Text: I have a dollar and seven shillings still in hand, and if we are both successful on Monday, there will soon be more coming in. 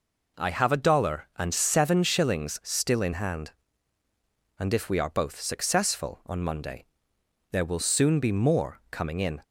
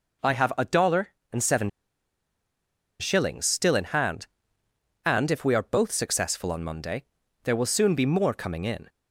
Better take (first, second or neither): first